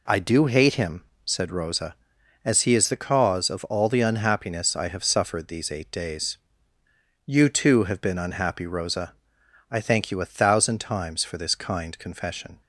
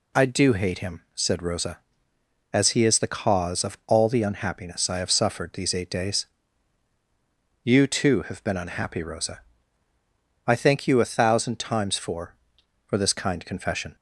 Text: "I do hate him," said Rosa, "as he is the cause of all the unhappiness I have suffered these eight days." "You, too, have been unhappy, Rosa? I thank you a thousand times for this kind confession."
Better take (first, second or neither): first